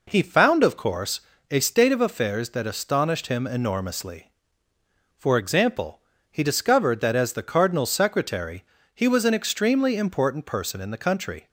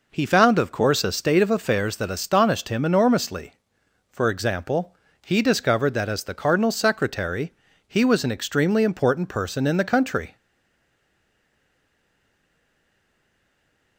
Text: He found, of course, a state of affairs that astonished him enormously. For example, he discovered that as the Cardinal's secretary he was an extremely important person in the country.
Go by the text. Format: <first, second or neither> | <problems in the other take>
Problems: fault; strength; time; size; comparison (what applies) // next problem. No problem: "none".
first | pauses between "secretary" and "he"; slight; at 7.5 s; 0.34 s long; slight in the first // stays silent after the last word; strong; from 10.3 s on; 3.6 s long